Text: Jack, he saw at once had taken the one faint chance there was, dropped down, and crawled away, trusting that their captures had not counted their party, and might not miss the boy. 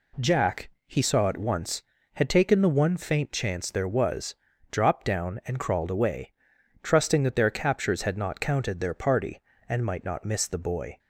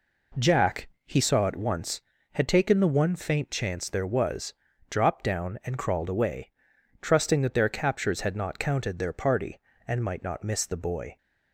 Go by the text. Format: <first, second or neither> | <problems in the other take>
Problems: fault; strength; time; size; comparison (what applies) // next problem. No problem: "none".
first | starts louder than the rest; until 1.5 s; 3.5 dB